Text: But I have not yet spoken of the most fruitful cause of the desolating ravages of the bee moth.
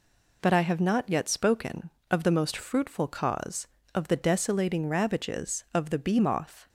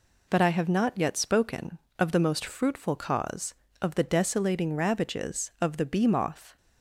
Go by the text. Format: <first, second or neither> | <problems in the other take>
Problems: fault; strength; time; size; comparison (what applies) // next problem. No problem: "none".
neither | none